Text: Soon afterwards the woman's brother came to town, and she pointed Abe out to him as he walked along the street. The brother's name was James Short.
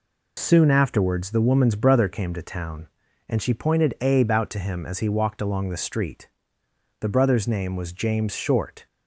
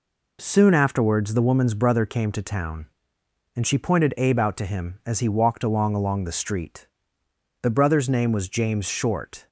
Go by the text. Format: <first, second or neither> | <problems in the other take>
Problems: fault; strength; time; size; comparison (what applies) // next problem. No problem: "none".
first | says "along" twice; at 5.9 s